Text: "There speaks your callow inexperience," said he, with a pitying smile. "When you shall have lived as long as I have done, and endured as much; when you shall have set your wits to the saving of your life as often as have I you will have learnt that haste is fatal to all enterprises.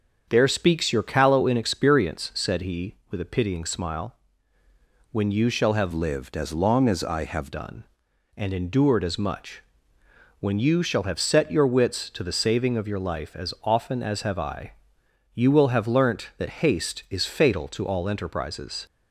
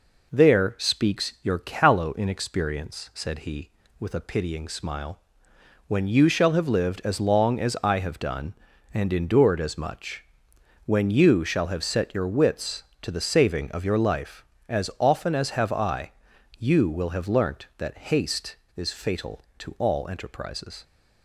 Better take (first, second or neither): second